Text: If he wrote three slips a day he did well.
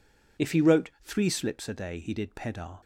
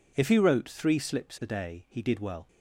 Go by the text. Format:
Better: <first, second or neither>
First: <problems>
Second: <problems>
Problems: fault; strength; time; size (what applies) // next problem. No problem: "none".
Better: second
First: says "pedar" for "well"; at 2.3 s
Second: none